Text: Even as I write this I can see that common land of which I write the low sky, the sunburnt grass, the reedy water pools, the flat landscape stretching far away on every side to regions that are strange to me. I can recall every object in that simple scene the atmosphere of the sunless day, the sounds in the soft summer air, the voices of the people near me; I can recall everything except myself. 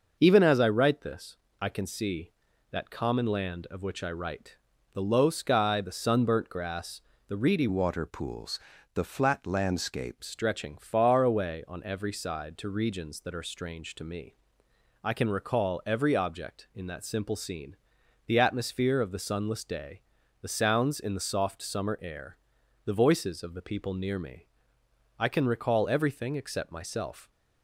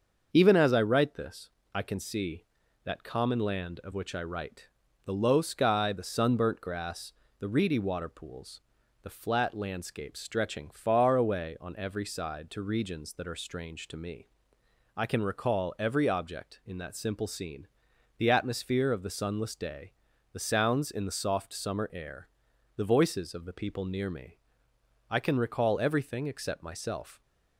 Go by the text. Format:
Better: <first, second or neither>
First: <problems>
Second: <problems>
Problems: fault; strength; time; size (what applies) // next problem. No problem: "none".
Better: second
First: starts louder than the rest; noticeable; until 1.2 s; 6 dB // pauses between "this" and "I"; slight; at 1.3 s; 0.26 s long // pauses between "write" and "the"; at 4.5 s; 0.38 s long // changes voice from "water" to "landscape"; from 7.6 to 10.2 s; 2.6 s long // pauses between "scene" and "the"; noticeable; at 17.7 s; 0.50 s long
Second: starts louder than the rest; until 1.3 s; 6.5 dB // pauses between "this" and "I"; slight; at 1.4 s; 0.26 s long // pauses between "write" and "the"; at 4.6 s; 0.38 s long // pauses between "scene" and "the"; noticeable; at 17.6 s; 0.50 s long